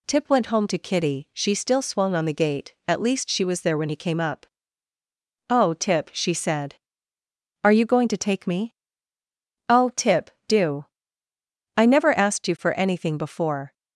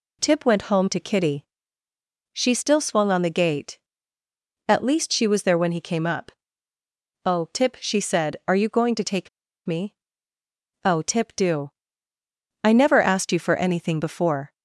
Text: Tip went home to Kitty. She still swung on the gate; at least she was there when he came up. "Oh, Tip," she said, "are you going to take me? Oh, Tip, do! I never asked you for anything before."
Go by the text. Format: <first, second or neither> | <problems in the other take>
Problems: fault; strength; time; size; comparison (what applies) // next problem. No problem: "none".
first | pauses between "take" and "me"; at 9.2 s; 0.39 s long